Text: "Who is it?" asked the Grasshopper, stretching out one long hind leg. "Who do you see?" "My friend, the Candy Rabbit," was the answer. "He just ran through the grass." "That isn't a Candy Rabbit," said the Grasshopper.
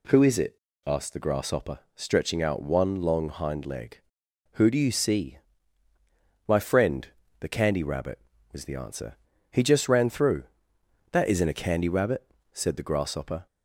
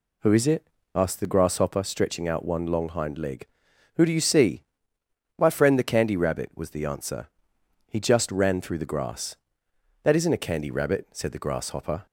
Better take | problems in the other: second | skips "the grass"; at 10.7 s

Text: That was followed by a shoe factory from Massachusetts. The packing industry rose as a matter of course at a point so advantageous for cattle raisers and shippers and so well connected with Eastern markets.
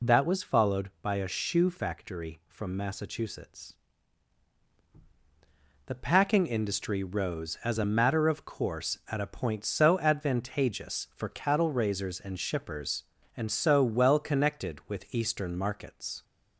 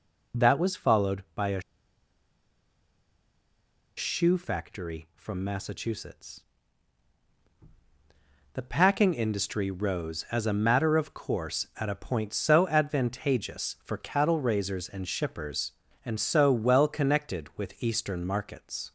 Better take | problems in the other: first | pauses between "a" and "shoe"; strong; at 1.6 s; 2.3 s long

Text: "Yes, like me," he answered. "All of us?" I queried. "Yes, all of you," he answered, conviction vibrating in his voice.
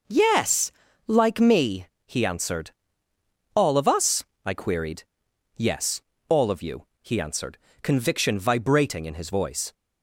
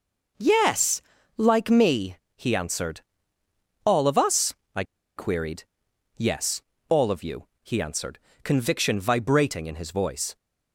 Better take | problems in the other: first | pauses between "I" and "queried"; slight; at 4.8 s; 0.33 s long

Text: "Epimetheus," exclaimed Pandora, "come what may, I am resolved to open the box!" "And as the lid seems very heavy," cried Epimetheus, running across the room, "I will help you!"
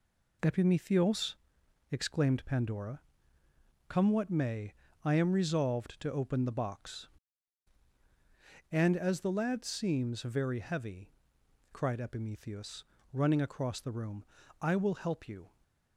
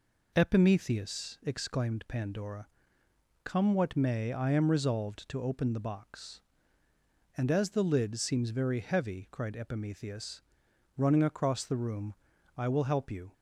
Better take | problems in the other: second | says "lad" for "lid"; at 9.3 s

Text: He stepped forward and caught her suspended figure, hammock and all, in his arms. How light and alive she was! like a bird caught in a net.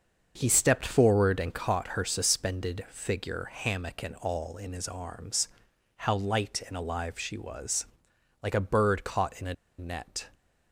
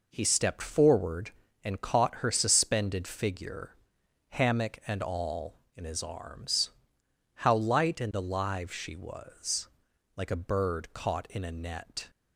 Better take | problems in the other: second | starts louder than the rest; until 1.3 s; 6.5 dB // pauses between "a" and "net"; slight; at 9.5 s; 0.24 s long

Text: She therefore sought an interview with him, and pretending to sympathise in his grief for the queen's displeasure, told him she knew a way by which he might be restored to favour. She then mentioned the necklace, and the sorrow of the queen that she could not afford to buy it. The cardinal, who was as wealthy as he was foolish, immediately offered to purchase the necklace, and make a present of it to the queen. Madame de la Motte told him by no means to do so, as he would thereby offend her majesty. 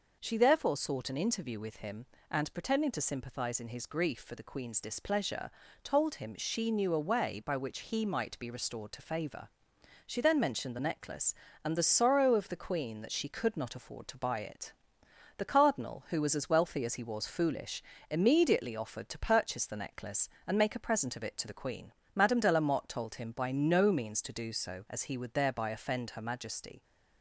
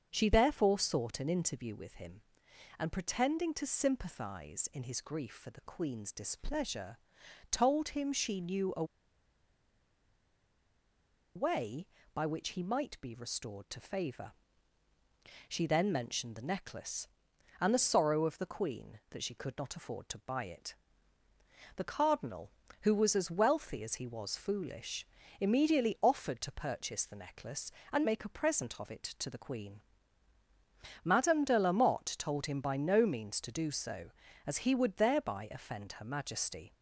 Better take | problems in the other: first | starts louder than the rest; until 1.1 s; 7 dB // pauses between "a" and "way"; strong; at 8.8 s; 2.5 s long

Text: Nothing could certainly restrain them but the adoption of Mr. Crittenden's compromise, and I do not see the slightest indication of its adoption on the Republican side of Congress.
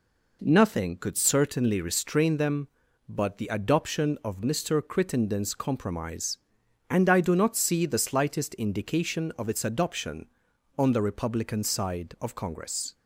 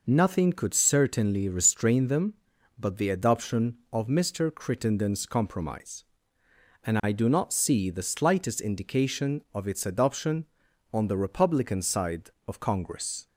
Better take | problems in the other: neither | none

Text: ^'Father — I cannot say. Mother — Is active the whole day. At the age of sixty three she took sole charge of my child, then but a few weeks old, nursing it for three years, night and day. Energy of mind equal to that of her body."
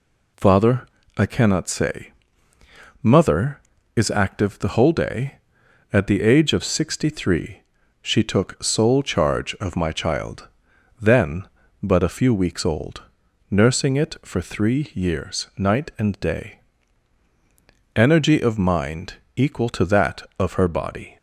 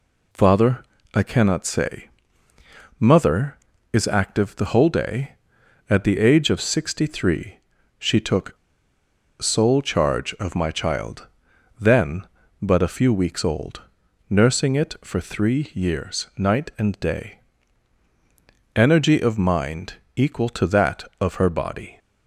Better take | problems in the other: first | pauses between "three" and "she"; at 7.5 s; 0.40 s long; also in the first // pauses between "took" and "sole"; noticeable; at 8.5 s; 0.83 s long // pauses between "mind" and "equal"; slight; at 19.9 s; 0.24 s long; slight in the first

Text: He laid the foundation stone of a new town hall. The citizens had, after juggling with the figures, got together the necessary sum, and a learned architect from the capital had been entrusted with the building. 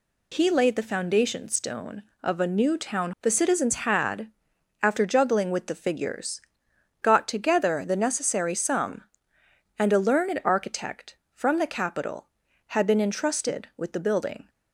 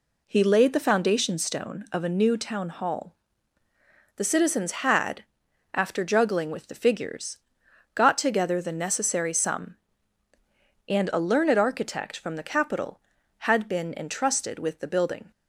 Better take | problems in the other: second | skips "hall"; at 3.1 s

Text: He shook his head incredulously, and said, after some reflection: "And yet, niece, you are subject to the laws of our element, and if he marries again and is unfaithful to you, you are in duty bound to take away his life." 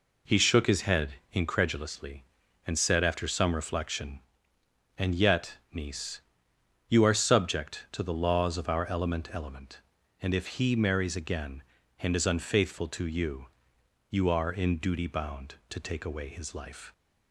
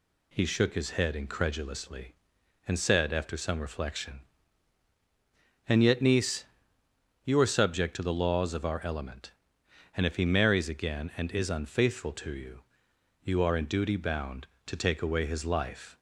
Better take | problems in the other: second | pauses between "head" and "incredulously"; slight; at 1.1 s; 0.16 s long // says "element" twice; at 9.3 s

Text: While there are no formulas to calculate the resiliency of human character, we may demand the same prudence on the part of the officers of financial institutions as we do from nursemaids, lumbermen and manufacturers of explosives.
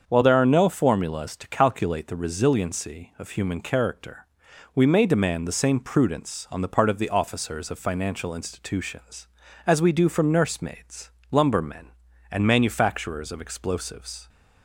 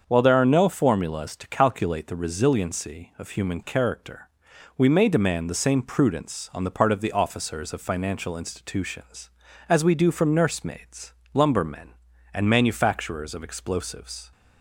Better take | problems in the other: neither | starts louder than the rest; the same in both

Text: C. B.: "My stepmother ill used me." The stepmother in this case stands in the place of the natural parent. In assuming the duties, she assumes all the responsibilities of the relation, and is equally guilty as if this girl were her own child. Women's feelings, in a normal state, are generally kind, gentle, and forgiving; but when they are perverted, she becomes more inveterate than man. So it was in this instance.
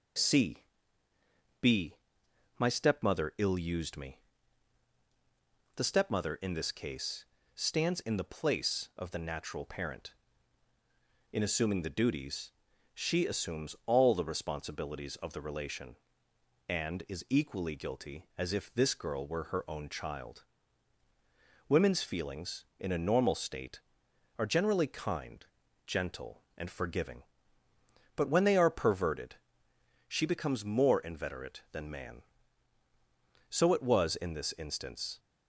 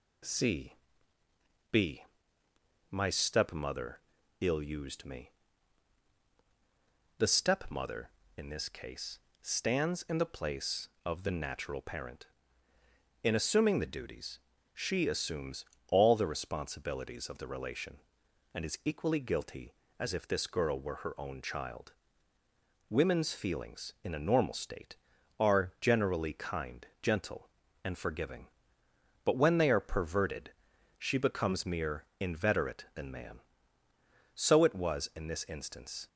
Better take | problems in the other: first | pauses between "stepmother" and "ill"; at 3.9 s; 0.40 s long // pauses between "case" and "stands"; slight; at 9.1 s; 0.22 s long; slight in the first // pauses between "assumes" and "all"; slight; at 15.6 s; 0.24 s long // says "mere" for "more"; at 31.6 s

